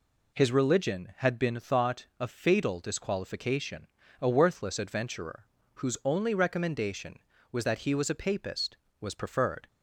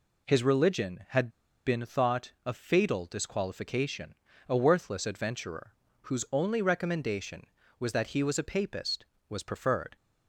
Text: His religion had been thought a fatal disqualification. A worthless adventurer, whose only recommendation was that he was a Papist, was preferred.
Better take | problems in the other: first | pauses between "had" and "been"; at 1.2 s; 0.36 s long

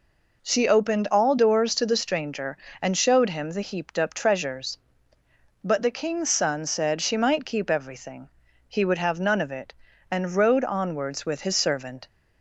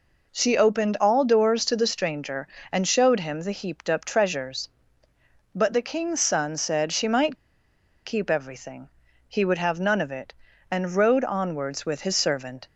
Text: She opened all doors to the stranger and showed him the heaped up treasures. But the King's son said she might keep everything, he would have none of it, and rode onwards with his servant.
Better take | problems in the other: first | pauses between "might" and "keep"; noticeable; at 7.3 s; 0.70 s long

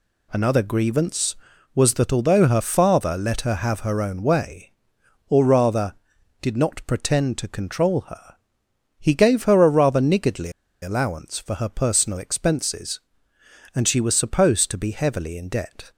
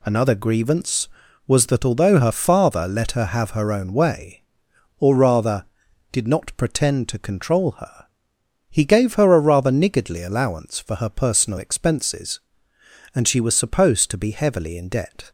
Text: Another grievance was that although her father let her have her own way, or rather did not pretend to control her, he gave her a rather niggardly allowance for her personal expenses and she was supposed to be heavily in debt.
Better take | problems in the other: second | pauses between "niggardly" and "allowance"; slight; at 10.5 s; 0.31 s long

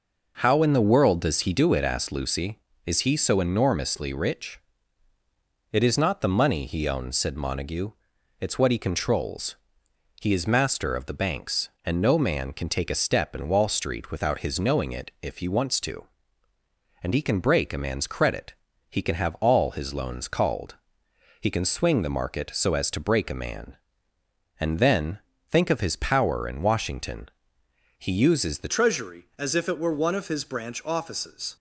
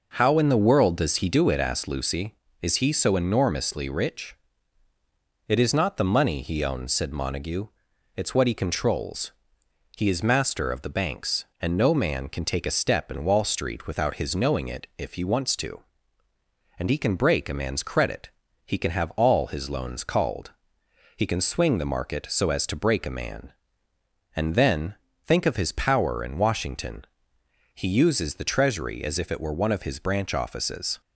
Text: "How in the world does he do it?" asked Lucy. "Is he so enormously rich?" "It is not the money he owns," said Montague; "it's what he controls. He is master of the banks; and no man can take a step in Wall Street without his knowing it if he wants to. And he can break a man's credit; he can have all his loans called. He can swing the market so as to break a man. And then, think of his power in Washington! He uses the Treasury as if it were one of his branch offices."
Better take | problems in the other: second | changes voice at "Treasury"; from 28.6 s on; 2.9 s long

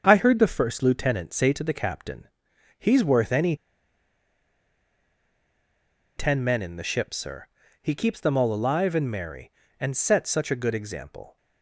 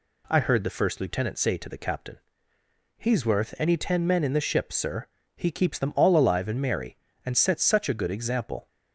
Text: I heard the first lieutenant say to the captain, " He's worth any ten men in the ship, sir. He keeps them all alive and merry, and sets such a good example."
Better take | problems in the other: second | starts louder than the rest; until 1.0 s; 7 dB // pauses between "any" and "ten"; strong; at 3.5 s; 2.6 s long

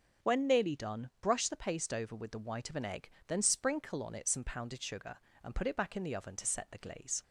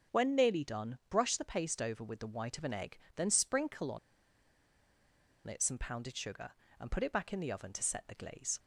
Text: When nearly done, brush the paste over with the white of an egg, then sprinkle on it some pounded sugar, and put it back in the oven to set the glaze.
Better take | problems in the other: first | starts louder than the rest; until 1.2 s; 7 dB; also in the first // pauses between "on" and "it"; strong; at 3.9 s; 1.4 s long

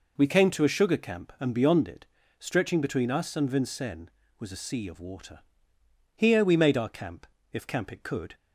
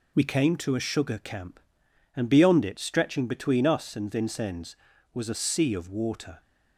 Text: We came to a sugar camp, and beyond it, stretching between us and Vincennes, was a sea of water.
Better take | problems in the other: second | goes on to say "Here we made our camp if camp it could"; strong; from 6.1 s on; 2.2 s long

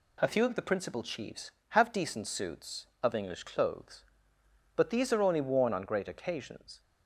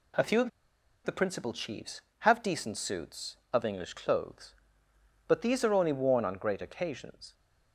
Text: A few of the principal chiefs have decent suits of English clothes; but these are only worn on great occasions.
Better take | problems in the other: first | pauses between "of" and "the"; noticeable; at 0.5 s; 0.55 s long

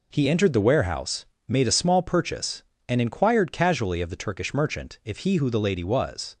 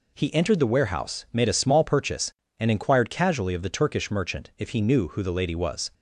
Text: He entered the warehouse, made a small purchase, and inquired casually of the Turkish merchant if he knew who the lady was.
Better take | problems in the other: second | skips "knew"; at 5.3 s

